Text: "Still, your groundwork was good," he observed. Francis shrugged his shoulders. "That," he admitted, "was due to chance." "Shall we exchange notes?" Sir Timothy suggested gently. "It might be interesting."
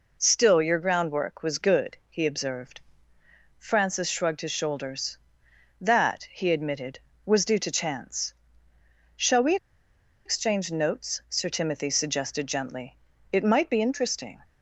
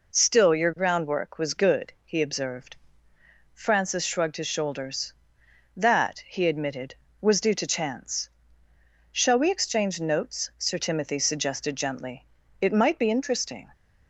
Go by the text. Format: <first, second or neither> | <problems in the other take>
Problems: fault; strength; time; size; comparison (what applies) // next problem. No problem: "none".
second | pauses between "we" and "exchange"; noticeable; at 9.5 s; 0.69 s long